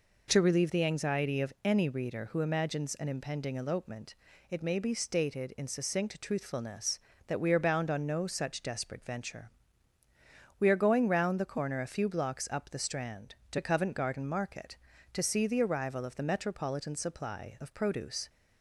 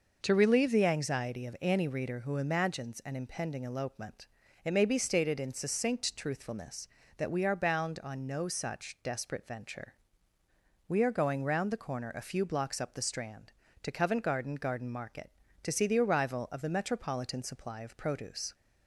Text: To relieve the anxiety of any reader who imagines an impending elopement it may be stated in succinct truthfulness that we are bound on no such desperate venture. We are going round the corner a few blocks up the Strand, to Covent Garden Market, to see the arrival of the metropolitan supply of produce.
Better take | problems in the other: first | pauses between "elopement" and "it"; at 4.2 s; 0.38 s long; also in the first // says "Garden" twice; at 14.5 s

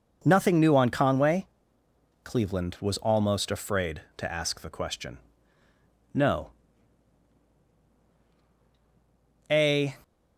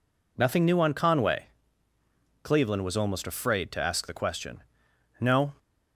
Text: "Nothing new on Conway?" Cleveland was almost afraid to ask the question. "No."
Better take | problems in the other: second | goes on to say "A"; slight; from 9.5 s on; 0.46 s long

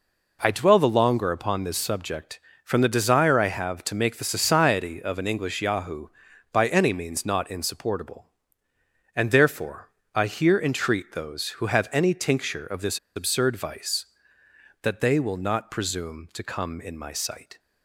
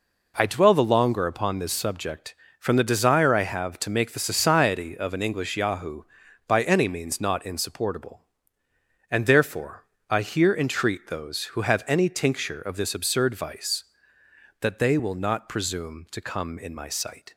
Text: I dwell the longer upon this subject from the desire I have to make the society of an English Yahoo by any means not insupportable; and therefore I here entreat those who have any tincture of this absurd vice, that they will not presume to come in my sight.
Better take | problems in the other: second | pauses between "therefore" and "I"; slight; at 9.8 s; 0.24 s long; slight in the second // pauses between "this" and "absurd"; slight; at 12.9 s; 0.17 s long

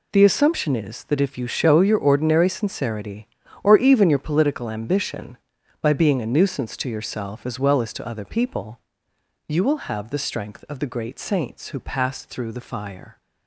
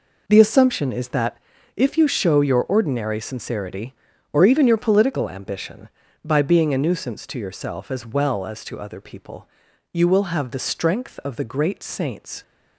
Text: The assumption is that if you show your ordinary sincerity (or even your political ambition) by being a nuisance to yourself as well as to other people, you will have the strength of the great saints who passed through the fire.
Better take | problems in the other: first | pauses between "that" and "if"; at 1.3 s; 0.40 s long // stops before "who passed through the fire"; at 12.4 s

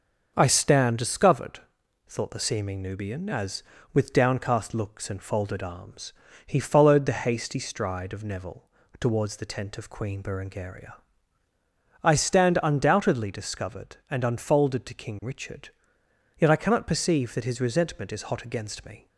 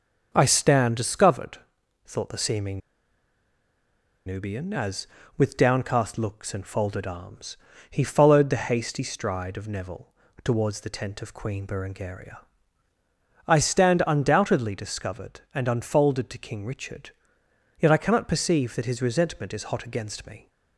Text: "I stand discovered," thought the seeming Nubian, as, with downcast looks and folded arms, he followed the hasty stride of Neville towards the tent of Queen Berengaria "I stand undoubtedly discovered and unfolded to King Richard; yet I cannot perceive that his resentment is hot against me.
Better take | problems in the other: first | pauses between "seeming" and "Nubian"; strong; at 2.7 s; 1.4 s long // pauses between "Neville" and "towards"; slight; at 10.1 s; 0.32 s long; slight in the first // pauses between "Berengaria" and "I"; at 12.3 s; 1.0 s long; also in the first

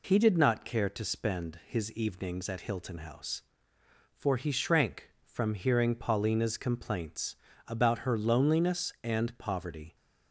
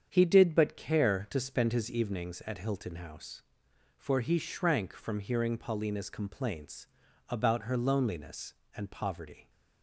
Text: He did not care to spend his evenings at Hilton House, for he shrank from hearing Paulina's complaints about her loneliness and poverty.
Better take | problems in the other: first | starts louder than the rest; strong; until 1.1 s; 8 dB // says "but" for "not"; at 0.5 s // pauses between "complaints" and "about"; at 6.8 s; 0.40 s long; slight in the first

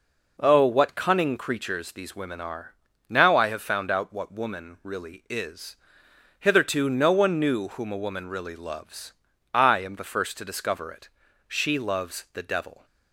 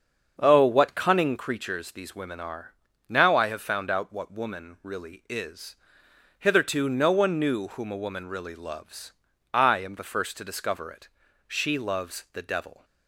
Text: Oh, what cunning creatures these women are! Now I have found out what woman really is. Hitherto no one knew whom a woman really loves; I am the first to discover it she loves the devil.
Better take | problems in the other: first | starts louder than the rest; until 1.5 s; 6.5 dB // pauses between "it" and "she"; at 11.0 s; 0.40 s long; also in the first

